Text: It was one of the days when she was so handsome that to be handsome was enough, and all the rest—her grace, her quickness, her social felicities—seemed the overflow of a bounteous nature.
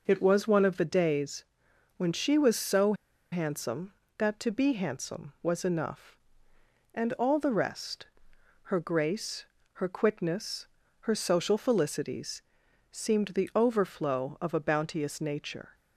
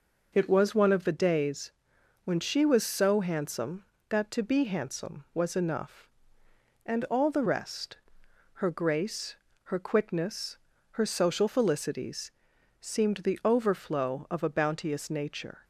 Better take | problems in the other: second | pauses between "days" and "when"; noticeable; at 1.4 s; 0.52 s long; noticeable in the second // pauses between "so" and "handsome"; at 2.9 s; 0.38 s long

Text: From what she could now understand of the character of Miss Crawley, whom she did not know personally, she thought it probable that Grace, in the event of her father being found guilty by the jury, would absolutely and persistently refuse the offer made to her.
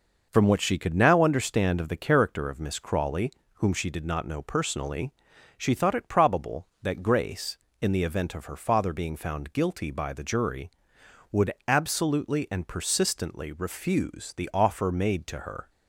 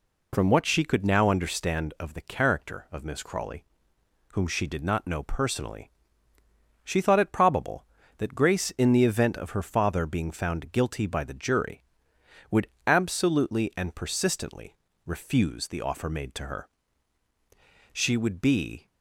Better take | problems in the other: first | pauses between "would" and "absolutely"; slight; at 12.6 s; 0.18 s long; slight in the first // pauses between "persistently" and "refuse"; slight; at 14.7 s; 0.32 s long // goes on to say "She would be"; noticeable; from 17.9 s on; 0.96 s long

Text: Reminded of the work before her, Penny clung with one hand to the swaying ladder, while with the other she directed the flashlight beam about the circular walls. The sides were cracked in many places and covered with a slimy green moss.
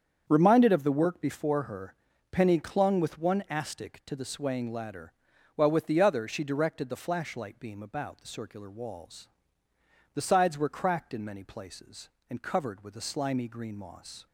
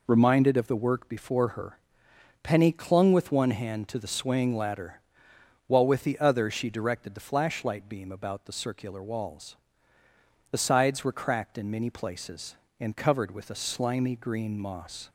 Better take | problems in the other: second | starts louder than the rest; strong; until 1.2 s; 7.5 dB // says "astic" for "hand"; at 3.4 s

